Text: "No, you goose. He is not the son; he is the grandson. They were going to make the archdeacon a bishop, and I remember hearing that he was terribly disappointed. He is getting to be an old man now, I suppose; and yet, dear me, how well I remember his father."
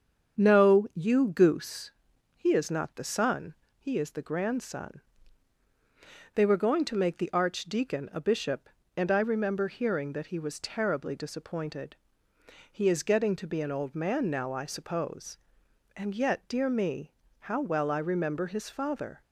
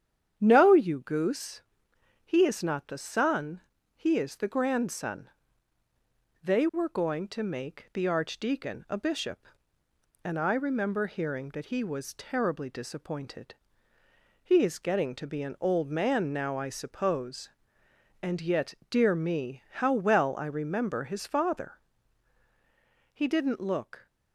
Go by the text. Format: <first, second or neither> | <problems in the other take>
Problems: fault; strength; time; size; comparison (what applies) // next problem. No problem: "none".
first | starts louder than the rest; strong; until 1.3 s; 9 dB; strong in the first // goes on to say "He didn't look"; noticeable; from 23.1 s on; 0.94 s long